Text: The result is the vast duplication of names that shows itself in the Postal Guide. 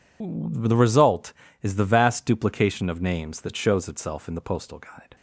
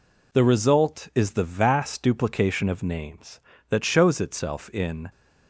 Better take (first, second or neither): first